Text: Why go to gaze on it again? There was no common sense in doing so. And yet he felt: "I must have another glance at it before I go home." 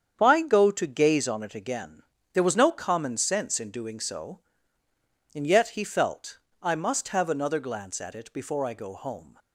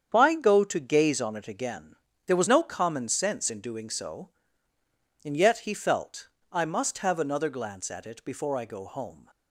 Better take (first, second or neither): neither